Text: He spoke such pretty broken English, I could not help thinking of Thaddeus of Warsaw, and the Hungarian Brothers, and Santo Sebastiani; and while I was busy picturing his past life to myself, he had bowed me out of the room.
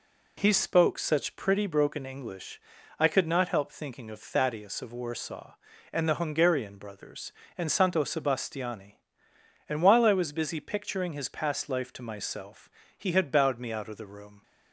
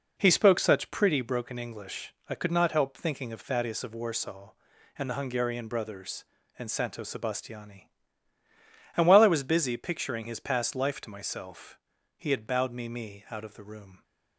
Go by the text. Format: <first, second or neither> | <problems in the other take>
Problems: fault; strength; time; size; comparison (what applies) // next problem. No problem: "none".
first | says "me" twice; at 12.8 s